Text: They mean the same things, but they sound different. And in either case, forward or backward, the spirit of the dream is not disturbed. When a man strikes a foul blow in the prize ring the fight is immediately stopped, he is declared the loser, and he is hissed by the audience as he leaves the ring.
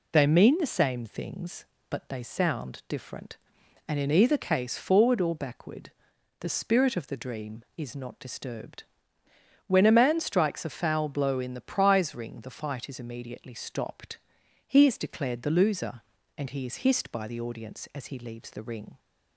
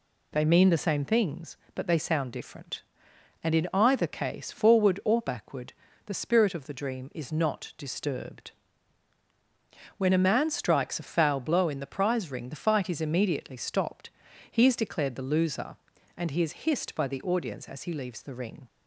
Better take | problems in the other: neither | none

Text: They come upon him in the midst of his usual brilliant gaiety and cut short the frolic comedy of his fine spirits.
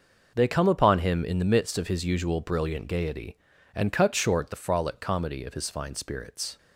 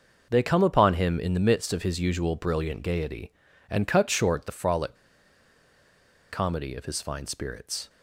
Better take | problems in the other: first | pauses between "frolic" and "comedy"; strong; at 4.9 s; 1.3 s long

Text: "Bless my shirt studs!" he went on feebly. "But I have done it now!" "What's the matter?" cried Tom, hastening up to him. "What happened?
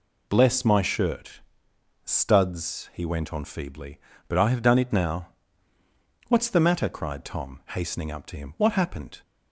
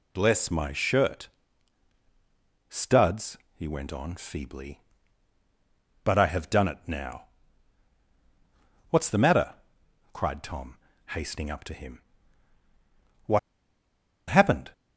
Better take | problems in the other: first | pauses between "shirt" and "studs"; strong; at 1.2 s; 1.4 s long; noticeable in the first // pauses between "What" and "happened"; noticeable; at 13.3 s; 0.90 s long

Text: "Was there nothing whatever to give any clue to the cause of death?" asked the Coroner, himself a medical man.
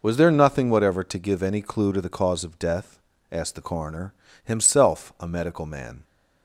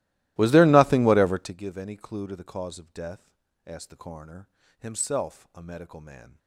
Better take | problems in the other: first | starts louder than the rest; strong; until 1.6 s; 16.5 dB

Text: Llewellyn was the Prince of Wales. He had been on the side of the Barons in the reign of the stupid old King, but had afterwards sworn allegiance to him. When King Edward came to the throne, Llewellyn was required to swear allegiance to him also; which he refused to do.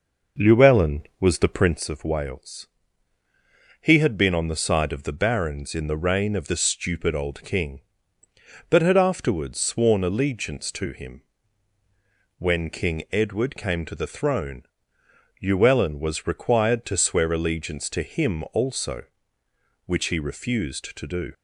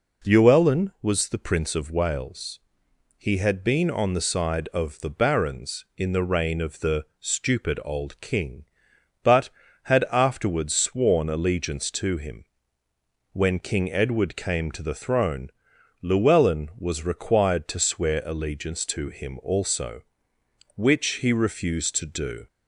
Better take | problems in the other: second | starts louder than the rest; noticeable; until 1.8 s; 5.5 dB

